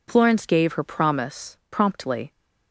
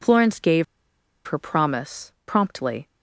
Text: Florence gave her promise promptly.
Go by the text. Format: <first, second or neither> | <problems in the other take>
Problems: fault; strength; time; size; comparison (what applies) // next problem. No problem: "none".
first | pauses between "gave" and "her"; noticeable; at 0.6 s; 0.63 s long